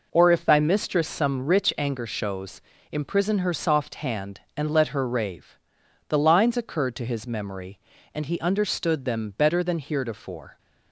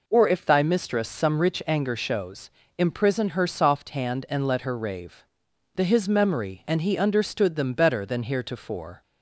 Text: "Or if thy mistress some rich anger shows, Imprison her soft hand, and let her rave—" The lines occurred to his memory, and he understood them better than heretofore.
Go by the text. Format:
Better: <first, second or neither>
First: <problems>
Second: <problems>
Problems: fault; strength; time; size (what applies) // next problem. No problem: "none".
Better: first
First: none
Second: skips "lines occurred to"; at 5.8 s